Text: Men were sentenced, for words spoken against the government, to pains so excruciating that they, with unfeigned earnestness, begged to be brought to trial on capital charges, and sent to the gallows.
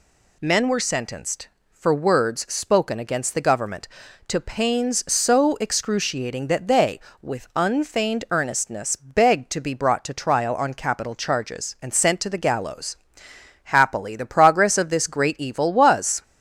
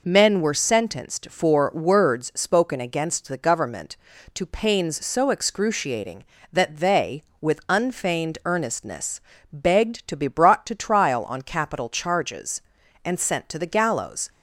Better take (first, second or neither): second